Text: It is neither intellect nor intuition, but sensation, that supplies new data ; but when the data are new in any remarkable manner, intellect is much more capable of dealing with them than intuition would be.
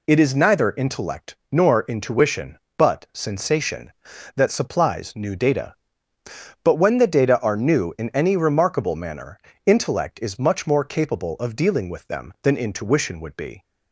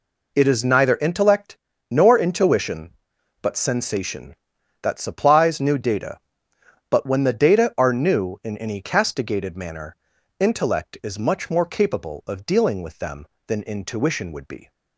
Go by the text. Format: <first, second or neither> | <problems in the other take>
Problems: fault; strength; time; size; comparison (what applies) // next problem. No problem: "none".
first | pauses between "intellect" and "nor"; slight; at 1.5 s; 0.32 s long; slight in the first // says "castigated" for "remarkable"; at 8.8 s